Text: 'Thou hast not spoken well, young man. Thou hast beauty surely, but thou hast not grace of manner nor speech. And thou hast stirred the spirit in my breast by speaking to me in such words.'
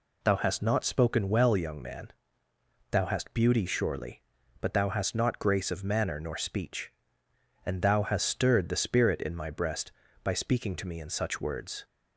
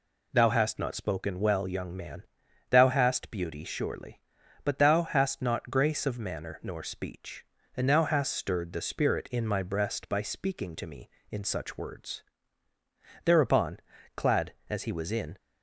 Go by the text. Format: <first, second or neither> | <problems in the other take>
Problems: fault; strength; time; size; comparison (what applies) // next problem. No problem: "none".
first | goes on to say "Thereupon clad as he was in"; strong; from 13.2 s on; 2.1 s long